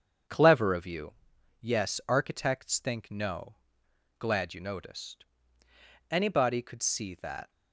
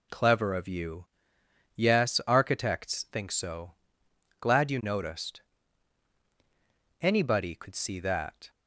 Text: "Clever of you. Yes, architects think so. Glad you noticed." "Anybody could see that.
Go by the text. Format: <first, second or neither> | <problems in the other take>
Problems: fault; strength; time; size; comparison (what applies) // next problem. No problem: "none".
second | starts louder than the rest; strong; until 1.7 s; 7.5 dB // says "no" for "so"; at 3.1 s